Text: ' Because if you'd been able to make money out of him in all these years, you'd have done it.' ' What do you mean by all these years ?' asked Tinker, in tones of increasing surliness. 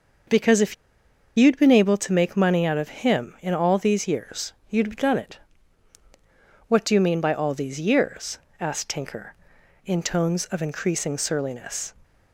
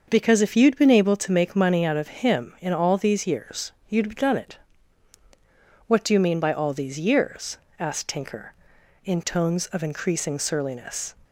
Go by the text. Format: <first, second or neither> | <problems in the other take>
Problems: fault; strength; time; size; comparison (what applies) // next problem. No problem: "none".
second | starts louder than the rest; until 1.9 s; 6.5 dB; also in the second // pauses between "if" and "you'd"; noticeable; at 0.7 s; 0.62 s long